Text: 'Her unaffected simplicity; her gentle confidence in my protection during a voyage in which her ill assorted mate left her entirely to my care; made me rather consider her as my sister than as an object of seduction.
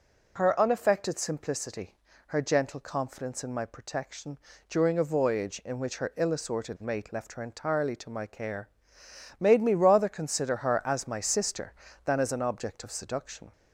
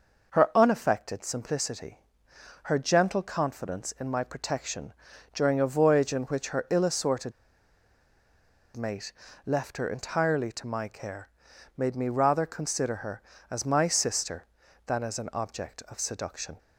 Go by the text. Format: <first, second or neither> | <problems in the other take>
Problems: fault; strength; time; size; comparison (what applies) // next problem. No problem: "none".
first | pauses between "protection" and "during"; at 4.9 s; 0.42 s long; slight in the first // pauses between "assorted" and "mate"; strong; at 7.3 s; 1.4 s long // pauses between "mate" and "left"; slight; at 9.1 s; 0.34 s long